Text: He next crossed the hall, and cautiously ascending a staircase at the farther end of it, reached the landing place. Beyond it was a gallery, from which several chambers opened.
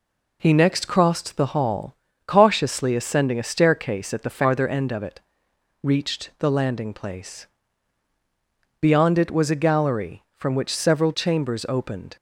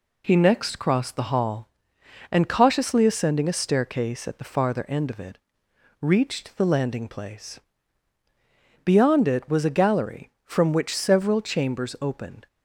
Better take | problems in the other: second | skips "and"; at 2.0 s

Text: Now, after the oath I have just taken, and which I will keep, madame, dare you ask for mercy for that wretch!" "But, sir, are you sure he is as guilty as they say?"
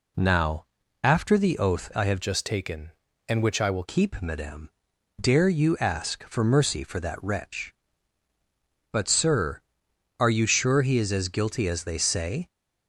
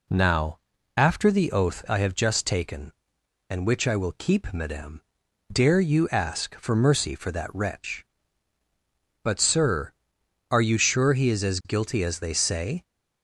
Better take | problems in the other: second | changes voice from "just" to "will"; from 2.2 to 3.8 s; 1.6 s long

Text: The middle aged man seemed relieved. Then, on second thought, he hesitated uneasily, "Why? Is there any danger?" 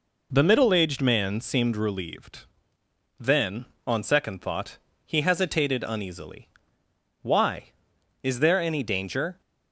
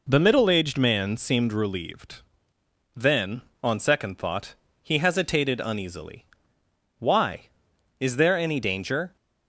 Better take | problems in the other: neither | none

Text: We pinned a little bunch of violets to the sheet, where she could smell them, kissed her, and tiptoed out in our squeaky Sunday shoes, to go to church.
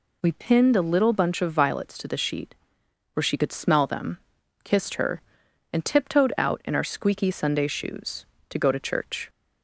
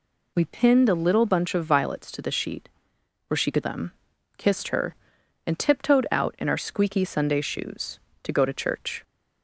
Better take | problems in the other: first | skips "smell"; at 3.6 s

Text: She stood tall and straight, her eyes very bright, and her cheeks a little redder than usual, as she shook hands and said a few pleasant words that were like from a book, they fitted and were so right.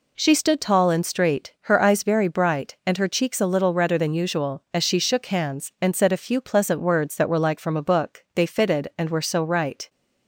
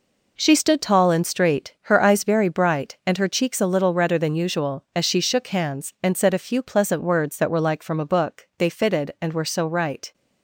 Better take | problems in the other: first | gets quieter; strong; throughout; 8 dB

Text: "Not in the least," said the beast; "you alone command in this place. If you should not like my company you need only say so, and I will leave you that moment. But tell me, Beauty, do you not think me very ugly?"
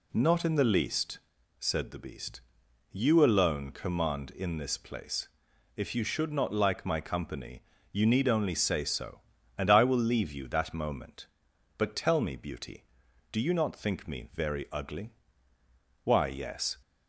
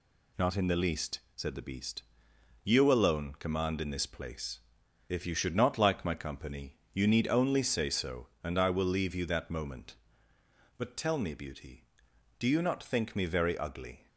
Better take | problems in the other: second | pauses between "company" and "you"; slight; at 7.6 s; 0.30 s long; slight in the second // goes on to say "Why yes"; noticeable; from 16.0 s on; 0.76 s long

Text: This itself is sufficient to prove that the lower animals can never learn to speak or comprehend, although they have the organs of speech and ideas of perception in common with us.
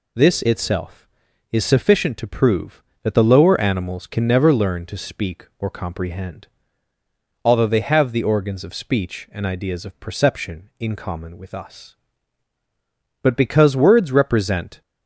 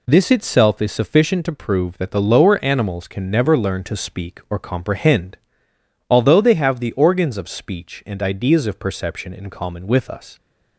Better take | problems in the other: second | goes on to say "But because words represent"; from 13.2 s on; 1.6 s long

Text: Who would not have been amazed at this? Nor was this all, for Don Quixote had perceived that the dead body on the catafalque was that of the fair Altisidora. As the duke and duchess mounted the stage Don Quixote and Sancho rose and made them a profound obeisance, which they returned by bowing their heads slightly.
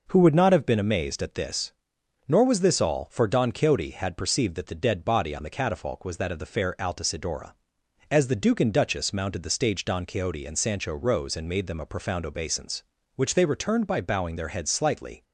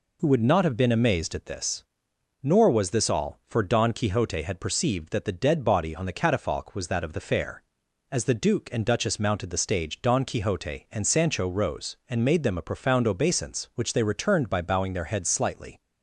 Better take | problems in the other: first | skips "Altisidora"; at 7.8 s

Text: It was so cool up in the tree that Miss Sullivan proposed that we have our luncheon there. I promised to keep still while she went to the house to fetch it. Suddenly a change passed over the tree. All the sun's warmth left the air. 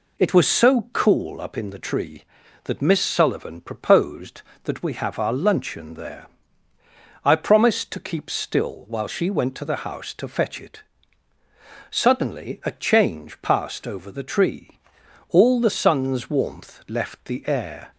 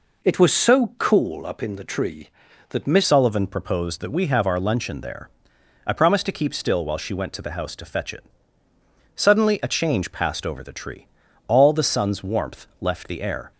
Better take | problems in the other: first | changes voice at "Sullivan"; from 3.0 s on; 10.5 s long

